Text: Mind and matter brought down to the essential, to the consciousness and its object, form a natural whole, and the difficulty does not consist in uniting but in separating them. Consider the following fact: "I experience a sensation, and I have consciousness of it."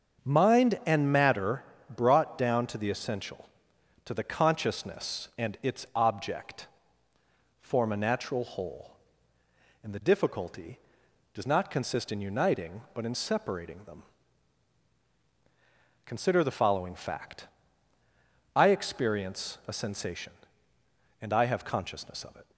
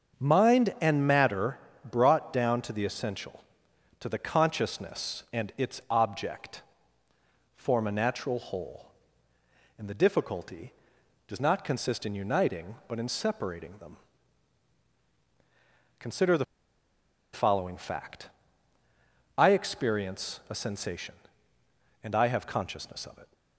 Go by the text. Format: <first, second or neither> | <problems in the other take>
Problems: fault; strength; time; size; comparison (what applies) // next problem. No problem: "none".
first | starts louder than the rest; until 1.2 s; 7 dB; also in the first // pauses between "matter" and "brought"; slight; at 1.5 s; 0.32 s long; slight in the first // pauses between "the" and "following"; noticeable; at 16.4 s; 0.88 s long